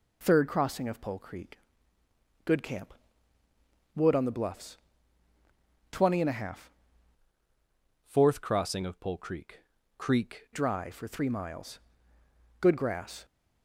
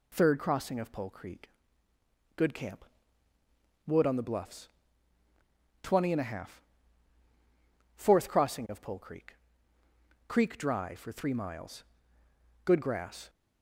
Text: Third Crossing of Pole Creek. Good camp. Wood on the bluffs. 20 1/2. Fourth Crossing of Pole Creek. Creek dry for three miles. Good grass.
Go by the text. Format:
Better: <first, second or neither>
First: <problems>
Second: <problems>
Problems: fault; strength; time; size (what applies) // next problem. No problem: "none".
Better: second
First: changes voice from "Fourth" to "Creek"; from 8.0 to 10.4 s; 2.4 s long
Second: none